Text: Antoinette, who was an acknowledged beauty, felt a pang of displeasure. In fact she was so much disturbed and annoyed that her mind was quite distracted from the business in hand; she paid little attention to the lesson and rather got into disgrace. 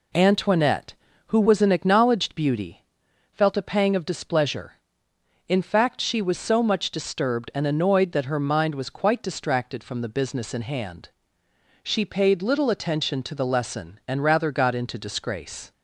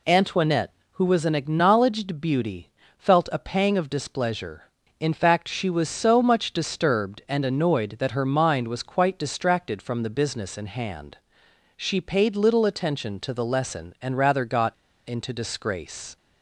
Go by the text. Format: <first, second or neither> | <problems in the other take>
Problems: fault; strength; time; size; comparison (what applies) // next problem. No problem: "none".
first | pauses between "got" and "into"; slight; at 14.7 s; 0.33 s long